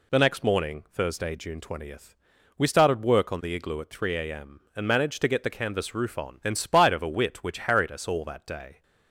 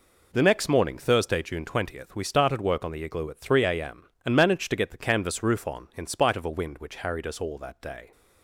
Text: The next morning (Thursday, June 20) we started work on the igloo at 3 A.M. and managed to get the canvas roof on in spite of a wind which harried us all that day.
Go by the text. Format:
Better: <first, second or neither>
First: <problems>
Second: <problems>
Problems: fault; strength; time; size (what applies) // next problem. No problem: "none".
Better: second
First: says "wit" for "wind"; at 7.0 s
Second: none